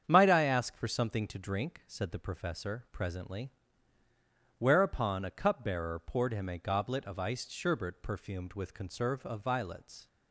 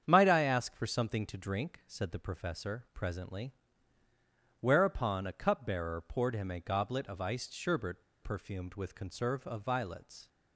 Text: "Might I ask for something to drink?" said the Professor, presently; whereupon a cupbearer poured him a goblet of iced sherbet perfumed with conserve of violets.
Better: first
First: starts louder than the rest; strong; until 1.0 s; 8 dB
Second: starts louder than the rest; strong; until 1.0 s; 8 dB // pauses between "sherbet" and "perfumed"; slight; at 8.0 s; 0.19 s long

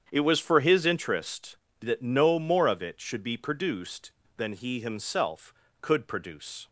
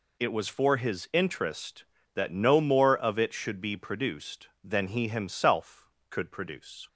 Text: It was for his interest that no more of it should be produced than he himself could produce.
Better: second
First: starts louder than the rest; strong; until 1.0 s; 8 dB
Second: none

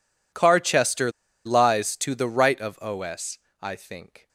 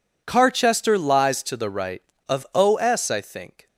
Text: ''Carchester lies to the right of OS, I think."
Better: second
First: pauses between "Carchester" and "lies"; at 1.1 s; 0.36 s long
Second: none

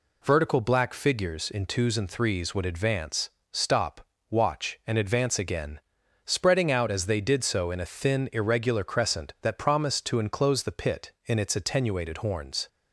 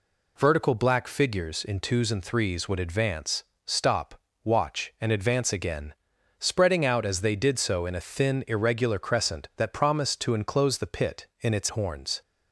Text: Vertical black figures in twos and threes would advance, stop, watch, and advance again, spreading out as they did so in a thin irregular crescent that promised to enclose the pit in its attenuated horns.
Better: first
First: none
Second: skips "attenuated"; at 11.7 s

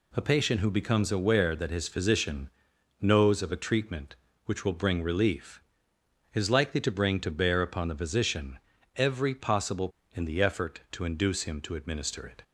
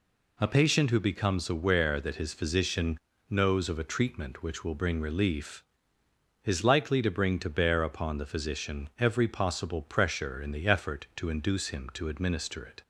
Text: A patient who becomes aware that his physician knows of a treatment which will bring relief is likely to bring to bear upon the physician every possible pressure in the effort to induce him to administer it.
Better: second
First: pauses between "physician" and "knows"; noticeable; at 2.5 s; 0.50 s long // pauses between "physician" and "every"; at 8.5 s; 0.38 s long // skips "pressure"; at 10.0 s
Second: pauses between "physician" and "knows"; slight; at 2.9 s; 0.30 s long

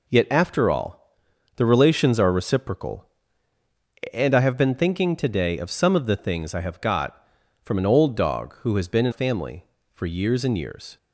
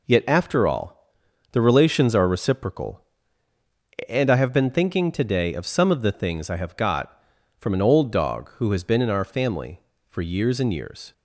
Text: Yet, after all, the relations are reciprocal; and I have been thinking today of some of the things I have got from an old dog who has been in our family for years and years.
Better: second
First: skips "our"; at 9.1 s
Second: none

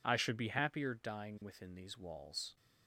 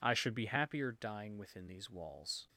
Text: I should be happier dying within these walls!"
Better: neither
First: none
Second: none

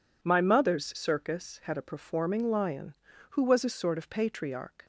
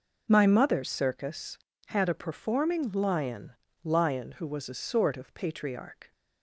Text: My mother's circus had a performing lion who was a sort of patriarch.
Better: first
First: none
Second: says "lion" twice; at 3.8 s

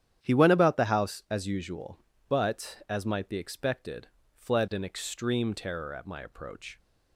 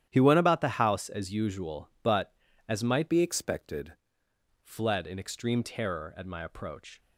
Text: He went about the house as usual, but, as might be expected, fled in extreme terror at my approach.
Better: first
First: starts louder than the rest; strong; until 1.2 s; 9.5 dB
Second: starts louder than the rest; strong; until 1.1 s; 11 dB // changes voice from "be" to "expected"; from 3.0 to 3.9 s; 0.9 s long

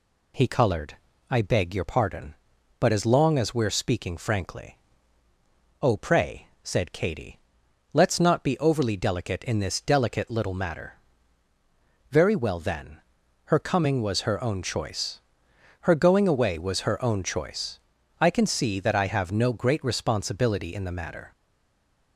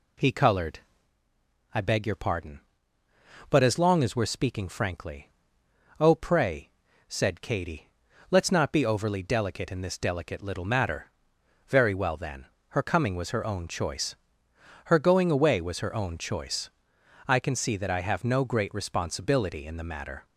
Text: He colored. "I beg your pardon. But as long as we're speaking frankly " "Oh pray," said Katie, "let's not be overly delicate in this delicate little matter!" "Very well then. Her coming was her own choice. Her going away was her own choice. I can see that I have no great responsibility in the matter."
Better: second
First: stays silent after the last word; slight; from 21.3 s on; 0.8 s long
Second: none

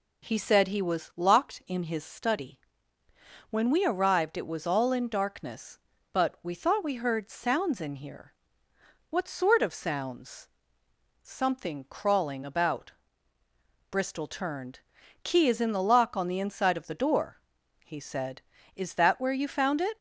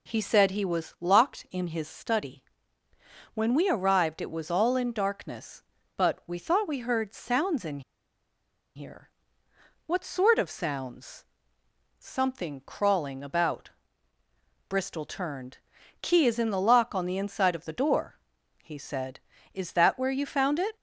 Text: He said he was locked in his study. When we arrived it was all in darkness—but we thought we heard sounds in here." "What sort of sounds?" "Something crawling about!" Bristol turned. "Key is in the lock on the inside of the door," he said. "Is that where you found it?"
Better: first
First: none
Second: pauses between "in" and "here"; noticeable; at 7.8 s; 0.95 s long

